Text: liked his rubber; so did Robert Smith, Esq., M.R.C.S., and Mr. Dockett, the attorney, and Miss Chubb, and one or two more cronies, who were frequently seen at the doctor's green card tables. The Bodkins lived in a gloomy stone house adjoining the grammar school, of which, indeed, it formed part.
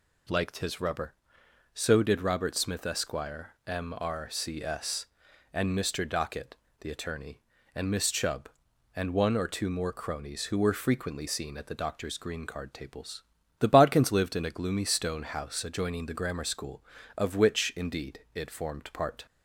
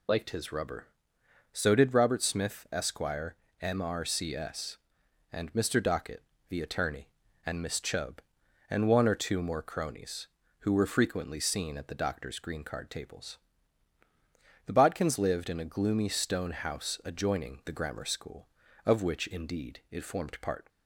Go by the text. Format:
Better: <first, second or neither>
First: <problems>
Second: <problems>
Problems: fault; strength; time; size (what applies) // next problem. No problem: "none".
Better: first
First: none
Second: loses the start of "liked"; at 0.0 s; 40 ms